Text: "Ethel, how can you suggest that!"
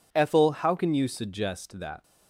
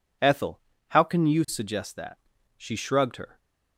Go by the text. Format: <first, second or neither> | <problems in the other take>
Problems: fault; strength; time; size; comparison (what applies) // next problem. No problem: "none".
first | goes on to say "She shrugged her"; noticeable; from 2.5 s on; 0.82 s long